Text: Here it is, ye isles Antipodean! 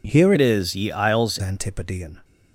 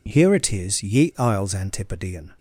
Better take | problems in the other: second | changes voice from "it" to "isles"; from 0.3 to 1.3 s; 1.0 s long

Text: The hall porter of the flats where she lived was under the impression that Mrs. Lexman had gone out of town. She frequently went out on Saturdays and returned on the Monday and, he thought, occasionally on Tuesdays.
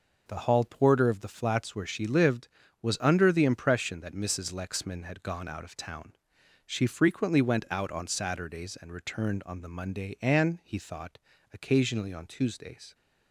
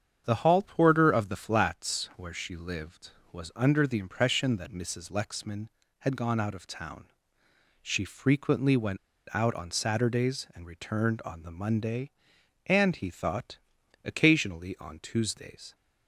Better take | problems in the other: first | starts louder than the rest; strong; until 1.2 s; 8 dB // pauses between "went" and "out"; at 8.9 s; 0.36 s long

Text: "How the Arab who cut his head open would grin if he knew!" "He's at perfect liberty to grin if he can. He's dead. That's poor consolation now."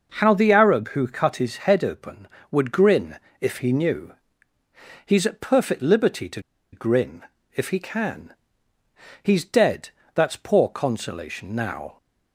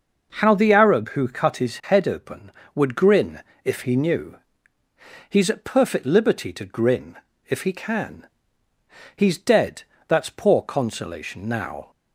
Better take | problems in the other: second | pauses between "grin" and "if"; slight; at 3.1 s; 0.22 s long; slight in the second // pauses between "to" and "grin"; slight; at 6.4 s; 0.32 s long // pauses between "grin" and "if"; slight; at 7.2 s; 0.32 s long; slight in the second

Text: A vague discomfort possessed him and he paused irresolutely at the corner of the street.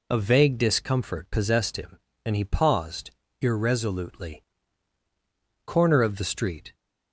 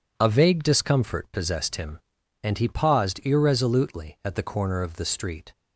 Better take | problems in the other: second | pauses between "paused" and "irresolutely"; slight; at 3.1 s; 0.30 s long // skips "at the"; at 5.0 s

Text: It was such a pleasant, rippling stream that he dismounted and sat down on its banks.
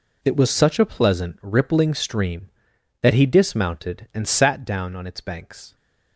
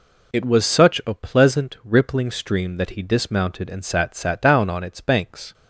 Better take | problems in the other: first | says "sat" twice; at 4.1 s

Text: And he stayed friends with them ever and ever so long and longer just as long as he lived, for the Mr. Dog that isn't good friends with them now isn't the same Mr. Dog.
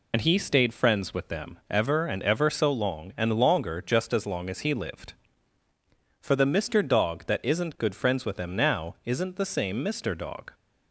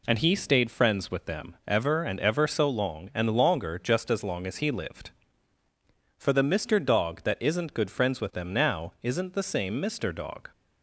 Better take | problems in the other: second | loses the start of "And"; at 0.1 s; 70 ms

